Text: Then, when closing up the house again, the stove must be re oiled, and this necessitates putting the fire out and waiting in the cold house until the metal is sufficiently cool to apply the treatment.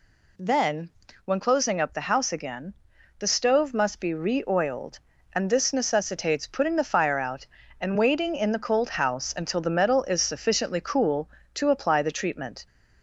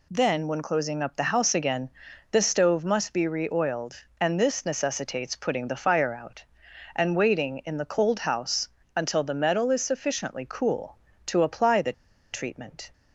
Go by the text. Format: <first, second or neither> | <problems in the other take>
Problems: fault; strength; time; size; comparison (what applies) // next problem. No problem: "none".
first | pauses between "house" and "until"; slight; at 8.6 s; 0.28 s long // pauses between "the" and "treatment"; at 11.9 s; 0.40 s long